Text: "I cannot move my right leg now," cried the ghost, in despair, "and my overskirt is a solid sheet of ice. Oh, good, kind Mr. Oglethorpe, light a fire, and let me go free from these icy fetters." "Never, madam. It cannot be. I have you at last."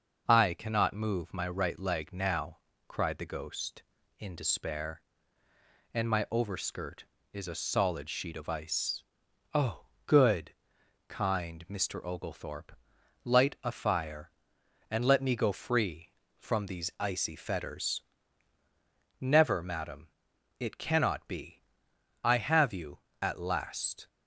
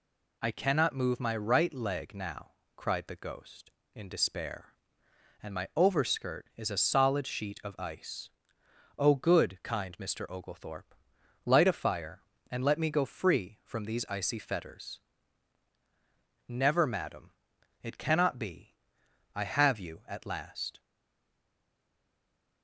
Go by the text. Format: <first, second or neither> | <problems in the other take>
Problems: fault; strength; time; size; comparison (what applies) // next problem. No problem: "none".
first | stays silent after the last word; noticeable; from 20.7 s on; 1.9 s long